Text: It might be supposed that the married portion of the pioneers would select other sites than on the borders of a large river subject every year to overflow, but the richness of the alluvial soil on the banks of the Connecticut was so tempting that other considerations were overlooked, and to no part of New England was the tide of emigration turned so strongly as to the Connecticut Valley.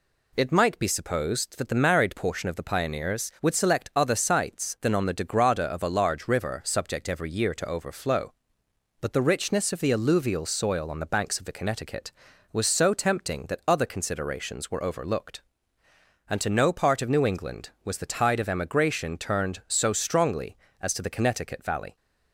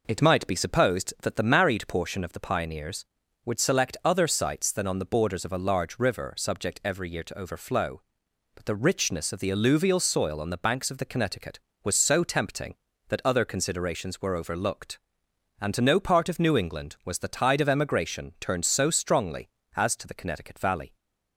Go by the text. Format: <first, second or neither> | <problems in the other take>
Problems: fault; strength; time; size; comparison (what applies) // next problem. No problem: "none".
second | says "degrada" for "borders"; at 5.1 s